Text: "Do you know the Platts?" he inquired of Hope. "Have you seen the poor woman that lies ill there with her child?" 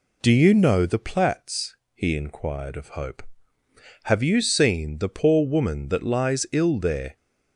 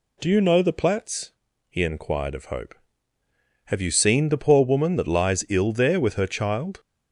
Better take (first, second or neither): second